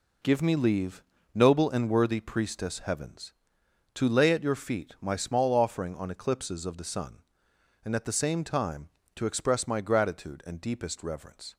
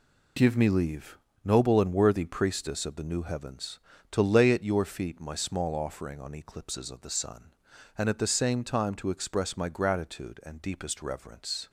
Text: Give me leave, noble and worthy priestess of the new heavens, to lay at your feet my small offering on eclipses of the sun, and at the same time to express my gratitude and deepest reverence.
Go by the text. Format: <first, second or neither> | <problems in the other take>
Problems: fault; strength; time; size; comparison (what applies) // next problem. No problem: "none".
second | skips "of the new"; at 2.7 s